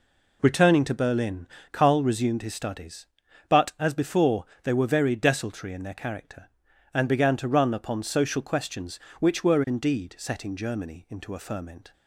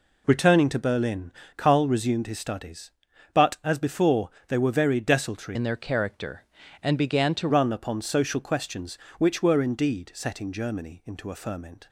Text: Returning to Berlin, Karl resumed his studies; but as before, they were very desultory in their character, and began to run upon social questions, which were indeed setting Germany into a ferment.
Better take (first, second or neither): first